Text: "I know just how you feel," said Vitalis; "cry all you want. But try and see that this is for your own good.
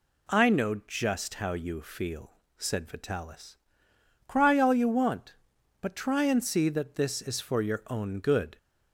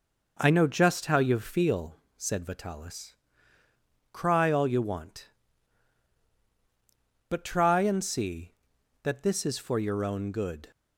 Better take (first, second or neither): neither